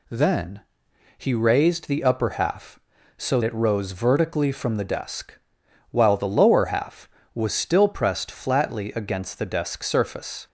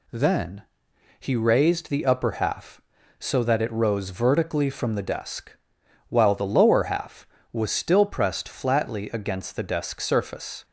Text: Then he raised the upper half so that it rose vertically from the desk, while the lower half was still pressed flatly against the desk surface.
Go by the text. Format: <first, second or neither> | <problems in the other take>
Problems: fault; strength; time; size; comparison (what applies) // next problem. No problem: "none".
second | pauses between "Then" and "he"; noticeable; at 0.6 s; 0.56 s long; noticeable in the second // skips "that"; at 3.4 s